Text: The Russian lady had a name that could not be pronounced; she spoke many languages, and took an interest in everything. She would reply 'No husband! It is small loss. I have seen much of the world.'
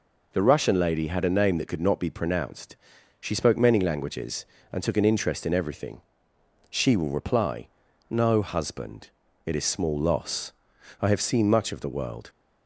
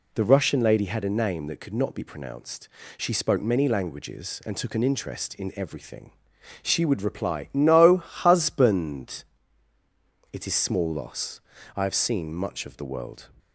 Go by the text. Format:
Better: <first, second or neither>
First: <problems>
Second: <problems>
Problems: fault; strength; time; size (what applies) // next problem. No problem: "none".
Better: second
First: says "will" for "would"; at 6.9 s // pauses between "reply" and "No"; noticeable; at 7.6 s; 0.46 s long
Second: none